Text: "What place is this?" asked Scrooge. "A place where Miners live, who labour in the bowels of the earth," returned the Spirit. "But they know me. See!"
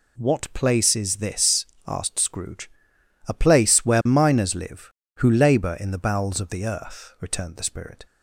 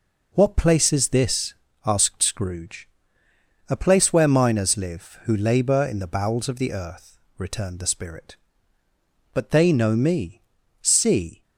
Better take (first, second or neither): second